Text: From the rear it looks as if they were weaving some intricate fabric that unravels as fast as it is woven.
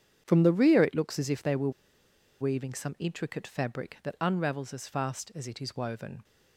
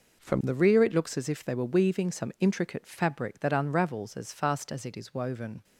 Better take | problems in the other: second | starts louder than the rest; strong; until 1.2 s; 8 dB // pauses between "were" and "weaving"; noticeable; at 1.6 s; 0.70 s long

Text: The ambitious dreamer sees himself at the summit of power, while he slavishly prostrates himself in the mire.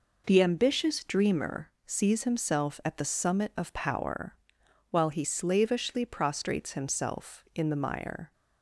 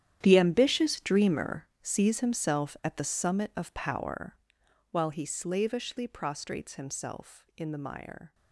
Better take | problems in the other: first | gets quieter; strong; throughout; 16 dB // pauses between "dreamer" and "sees"; slight; at 1.6 s; 0.16 s long; slight in the first

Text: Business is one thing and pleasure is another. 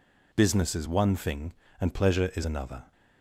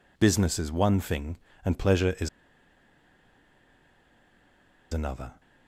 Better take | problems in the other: first | pauses between "is" and "another"; strong; at 2.2 s; 2.6 s long

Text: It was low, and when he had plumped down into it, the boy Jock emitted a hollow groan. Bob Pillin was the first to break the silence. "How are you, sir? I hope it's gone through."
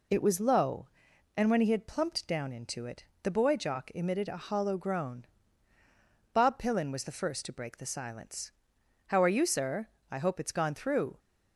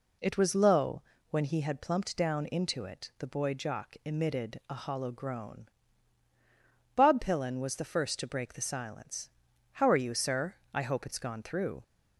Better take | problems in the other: first | skips "and"; at 1.1 s

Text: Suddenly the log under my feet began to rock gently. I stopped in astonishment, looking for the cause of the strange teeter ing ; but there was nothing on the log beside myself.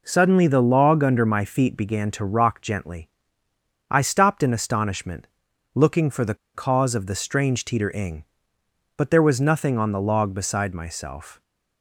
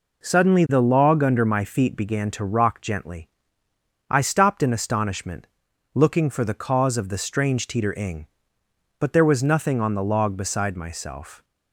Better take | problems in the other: second | pauses between "the" and "cause"; slight; at 6.3 s; 0.20 s long

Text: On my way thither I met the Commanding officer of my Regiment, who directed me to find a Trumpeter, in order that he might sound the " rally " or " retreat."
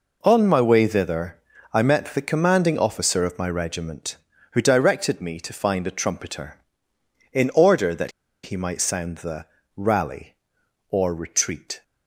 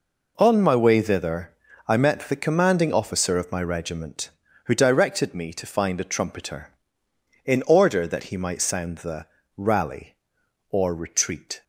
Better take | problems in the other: second | pauses between "thither" and "I"; slight; at 1.3 s; 0.34 s long; slight in the second // pauses between "that" and "he"; slight; at 8.1 s; 0.33 s long

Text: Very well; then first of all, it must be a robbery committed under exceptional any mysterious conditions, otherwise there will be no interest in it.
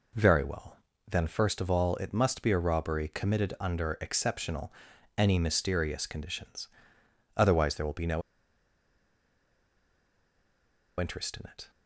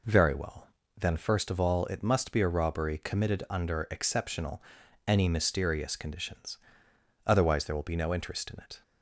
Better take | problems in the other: second | pauses between "exceptional" and "any"; noticeable; at 4.7 s; 0.46 s long; noticeable in the second // pauses between "no" and "interest"; strong; at 8.2 s; 2.7 s long

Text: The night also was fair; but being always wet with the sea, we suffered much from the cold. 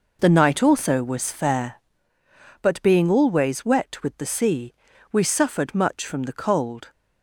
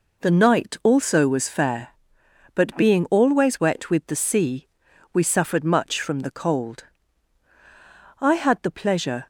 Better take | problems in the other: first | goes on to say "I had the pleasure"; noticeable; from 8.1 s on; 1.1 s long

